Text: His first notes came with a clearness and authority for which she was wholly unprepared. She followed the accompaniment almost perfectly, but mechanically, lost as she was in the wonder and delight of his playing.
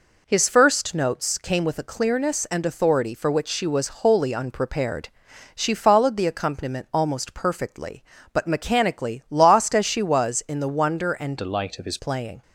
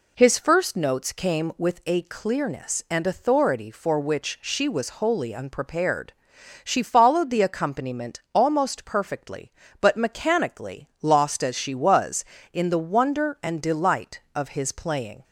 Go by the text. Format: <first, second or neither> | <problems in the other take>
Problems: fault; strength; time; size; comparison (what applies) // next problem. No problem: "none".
second | changes voice from "delight" to "his"; from 11.3 to 11.9 s; 0.6 s long